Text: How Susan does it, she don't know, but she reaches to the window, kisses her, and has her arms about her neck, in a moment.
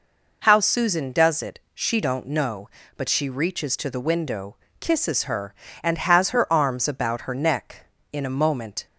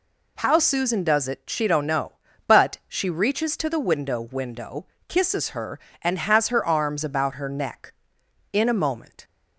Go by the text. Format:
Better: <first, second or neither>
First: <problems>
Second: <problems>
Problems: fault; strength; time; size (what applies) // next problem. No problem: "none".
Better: first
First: none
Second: says "window" twice; at 4.1 s